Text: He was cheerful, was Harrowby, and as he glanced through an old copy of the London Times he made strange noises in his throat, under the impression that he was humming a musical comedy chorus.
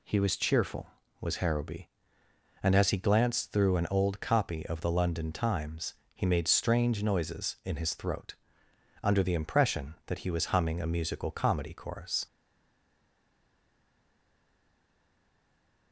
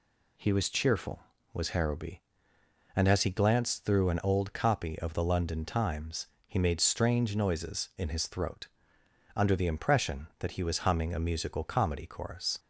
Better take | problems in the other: second | pauses between "Times" and "he"; slight; at 5.9 s; 0.20 s long; slight in the second // stays silent after the last word; strong; from 12.2 s on; 3.7 s long

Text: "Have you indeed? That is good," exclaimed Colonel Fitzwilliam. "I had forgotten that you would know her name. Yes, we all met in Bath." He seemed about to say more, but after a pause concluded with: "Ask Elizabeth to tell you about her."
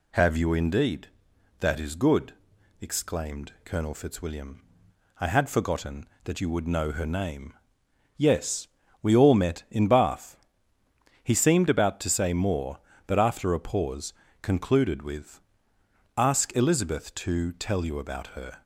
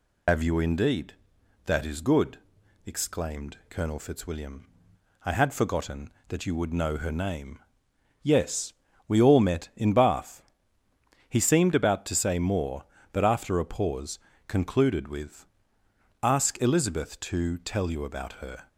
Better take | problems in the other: first | loses the start of "Have"; at 0.2 s; 85 ms // pauses between "pause" and "concluded"; slight; at 14.1 s; 0.30 s long; slight in the first

